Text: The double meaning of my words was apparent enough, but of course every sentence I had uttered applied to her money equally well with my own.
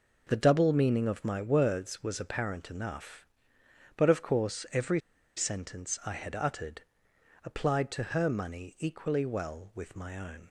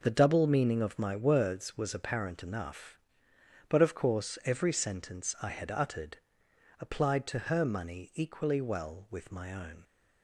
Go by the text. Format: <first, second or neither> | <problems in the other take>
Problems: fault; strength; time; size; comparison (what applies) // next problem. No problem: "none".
second | pauses between "every" and "sentence"; at 4.9 s; 0.36 s long // pauses between "uttered" and "applied"; noticeable; at 6.8 s; 0.60 s long; noticeable in the second